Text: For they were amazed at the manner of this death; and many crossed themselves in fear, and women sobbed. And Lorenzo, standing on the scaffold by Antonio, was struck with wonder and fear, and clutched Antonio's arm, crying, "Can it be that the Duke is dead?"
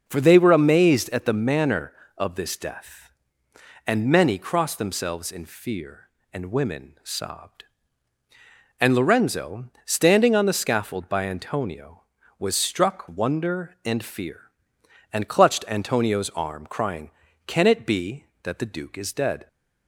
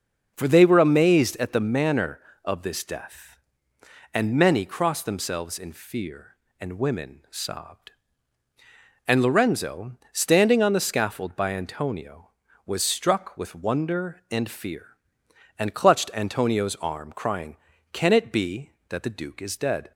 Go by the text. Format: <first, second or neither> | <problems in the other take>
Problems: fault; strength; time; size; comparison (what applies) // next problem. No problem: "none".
second | skips "with"; at 13.0 s